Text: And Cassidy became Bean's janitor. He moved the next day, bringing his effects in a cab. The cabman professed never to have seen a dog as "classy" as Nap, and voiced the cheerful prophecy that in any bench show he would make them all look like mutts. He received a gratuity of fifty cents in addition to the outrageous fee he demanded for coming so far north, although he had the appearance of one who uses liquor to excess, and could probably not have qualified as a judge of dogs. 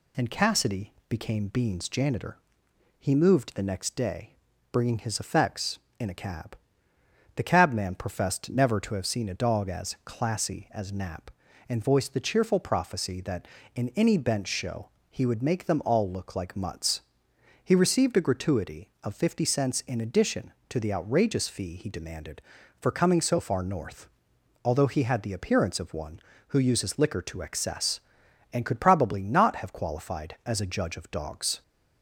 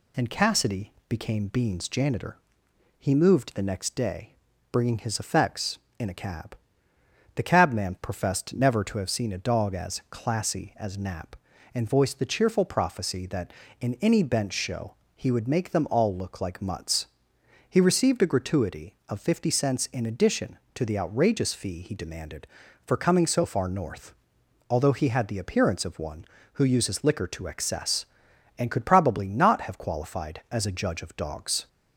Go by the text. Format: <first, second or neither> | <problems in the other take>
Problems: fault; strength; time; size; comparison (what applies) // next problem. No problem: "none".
neither | pauses between "Cassidy" and "became"; slight; the same in both // pauses between "show" and "he"; slight; the same in both